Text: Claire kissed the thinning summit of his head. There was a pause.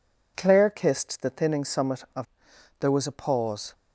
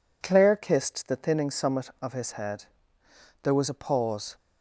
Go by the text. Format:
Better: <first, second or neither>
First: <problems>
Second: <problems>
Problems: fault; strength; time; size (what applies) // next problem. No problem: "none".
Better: second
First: skips "his head"; at 2.5 s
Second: none